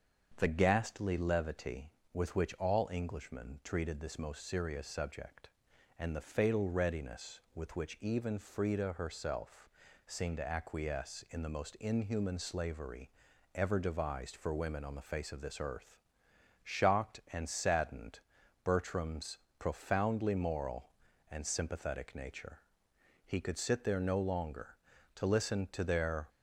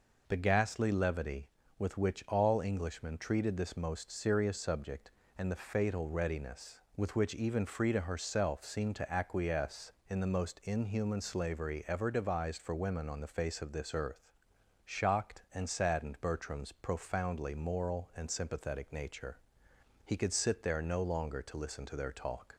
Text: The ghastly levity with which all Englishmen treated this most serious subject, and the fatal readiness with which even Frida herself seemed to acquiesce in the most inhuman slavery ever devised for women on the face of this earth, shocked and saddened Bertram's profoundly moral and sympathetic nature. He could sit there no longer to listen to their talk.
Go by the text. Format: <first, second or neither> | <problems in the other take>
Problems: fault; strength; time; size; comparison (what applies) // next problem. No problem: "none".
second | starts louder than the rest; strong; until 1.3 s; 7 dB // pauses between "herself" and "seemed"; at 9.6 s; 0.38 s long // pauses between "slavery" and "ever"; at 13.1 s; 0.44 s long // pauses between "saddened" and "Bertram's"; noticeable; at 18.1 s; 0.46 s long // pauses between "Bertram's" and "profoundly"; slight; at 19.3 s; 0.22 s long // stops before "talk"; at 26.2 s